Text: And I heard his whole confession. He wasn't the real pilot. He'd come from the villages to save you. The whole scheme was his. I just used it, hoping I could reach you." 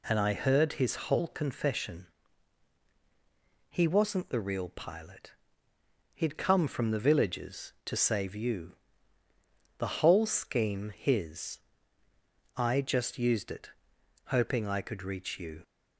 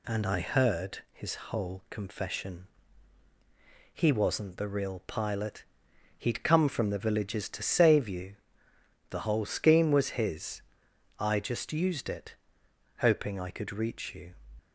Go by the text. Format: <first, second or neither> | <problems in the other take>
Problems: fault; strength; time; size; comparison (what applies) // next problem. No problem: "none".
second | skips "was"; at 10.9 s